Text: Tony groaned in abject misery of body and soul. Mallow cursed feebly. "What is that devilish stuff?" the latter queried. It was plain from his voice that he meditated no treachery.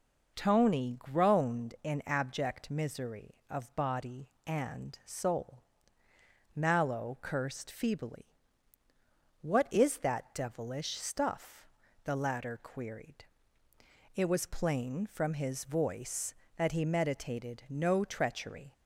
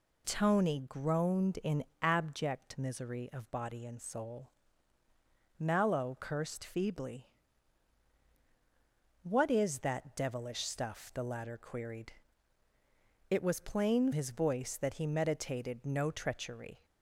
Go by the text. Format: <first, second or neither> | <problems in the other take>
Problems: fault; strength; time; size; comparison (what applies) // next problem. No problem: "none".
first | pauses between "in" and "abject"; slight; at 1.8 s; 0.18 s long // skips "from"; at 14.1 s